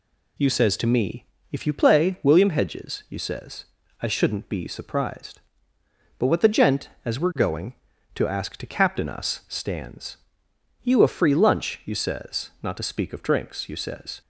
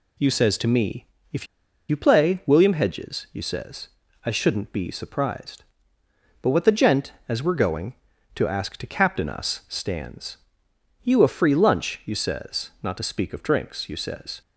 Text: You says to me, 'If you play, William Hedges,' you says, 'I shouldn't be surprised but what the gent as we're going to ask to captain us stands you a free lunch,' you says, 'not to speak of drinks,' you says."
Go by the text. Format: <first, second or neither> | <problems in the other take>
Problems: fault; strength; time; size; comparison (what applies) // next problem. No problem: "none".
first | pauses between "If" and "you"; at 1.4 s; 0.42 s long // pauses between "stands" and "you"; noticeable; at 10.3 s; 0.66 s long; noticeable in the first